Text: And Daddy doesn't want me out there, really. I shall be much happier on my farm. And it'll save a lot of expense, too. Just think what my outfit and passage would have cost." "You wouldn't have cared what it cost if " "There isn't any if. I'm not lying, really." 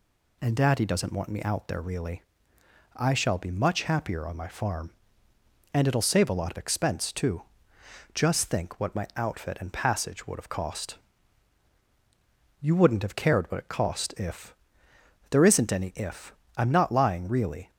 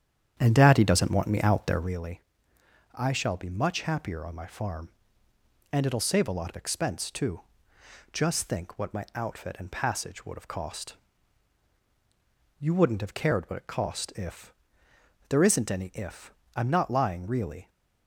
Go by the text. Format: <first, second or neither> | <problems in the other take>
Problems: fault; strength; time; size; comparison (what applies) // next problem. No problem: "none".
first | starts louder than the rest; strong; until 2.0 s; 9 dB